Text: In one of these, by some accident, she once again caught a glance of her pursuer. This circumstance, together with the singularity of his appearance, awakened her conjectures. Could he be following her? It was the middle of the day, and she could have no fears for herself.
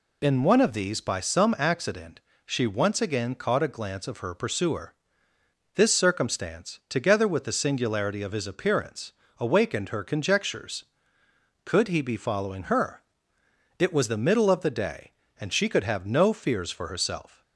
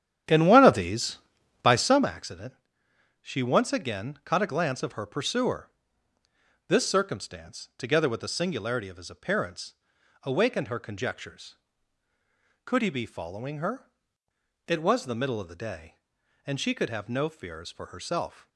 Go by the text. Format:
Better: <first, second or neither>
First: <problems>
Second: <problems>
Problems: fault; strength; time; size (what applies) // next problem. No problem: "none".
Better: first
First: none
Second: starts louder than the rest; strong; until 2.1 s; 10.5 dB